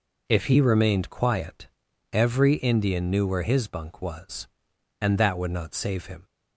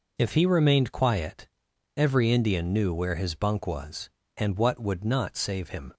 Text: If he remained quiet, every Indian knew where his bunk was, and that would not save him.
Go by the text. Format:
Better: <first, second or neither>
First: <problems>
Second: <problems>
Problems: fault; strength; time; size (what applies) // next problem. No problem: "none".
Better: first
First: none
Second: says "what" for "that"; at 4.5 s